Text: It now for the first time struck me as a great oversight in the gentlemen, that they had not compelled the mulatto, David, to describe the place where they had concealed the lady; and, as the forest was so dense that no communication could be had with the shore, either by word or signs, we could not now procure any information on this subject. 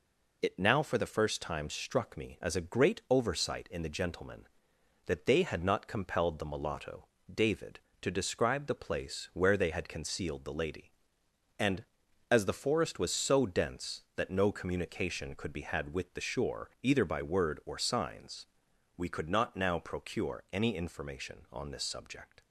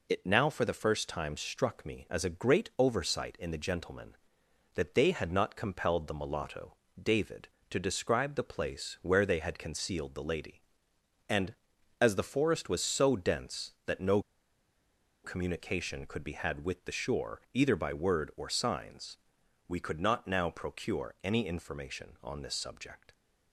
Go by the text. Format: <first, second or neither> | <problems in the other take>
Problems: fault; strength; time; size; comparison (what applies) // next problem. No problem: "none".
first | pauses between "no" and "communication"; at 14.2 s; 1.0 s long